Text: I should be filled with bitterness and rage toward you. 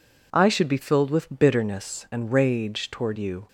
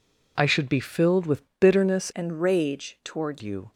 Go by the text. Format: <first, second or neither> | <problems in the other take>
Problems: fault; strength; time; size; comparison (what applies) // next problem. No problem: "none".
first | pauses between "with" and "bitterness"; slight; at 1.4 s; 0.18 s long // changes voice from "and" to "toward"; from 2.1 to 3.4 s; 1.3 s long